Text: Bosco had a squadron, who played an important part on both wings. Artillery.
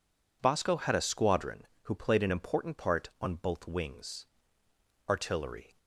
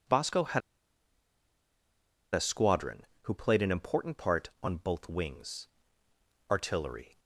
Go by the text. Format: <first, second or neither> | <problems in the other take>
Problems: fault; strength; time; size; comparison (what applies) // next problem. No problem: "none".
first | pauses between "had" and "a"; strong; at 0.6 s; 1.7 s long